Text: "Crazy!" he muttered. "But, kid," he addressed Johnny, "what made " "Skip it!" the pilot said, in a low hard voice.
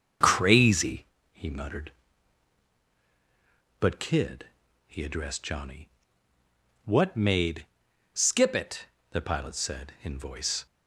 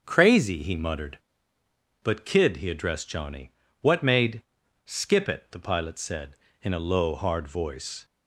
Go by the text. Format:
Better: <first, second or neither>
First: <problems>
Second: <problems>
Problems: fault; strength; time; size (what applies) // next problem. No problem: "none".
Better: second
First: starts louder than the rest; strong; until 1.4 s; 7 dB // skips "a low hard"; at 10.1 s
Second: starts louder than the rest; until 1.0 s; 7 dB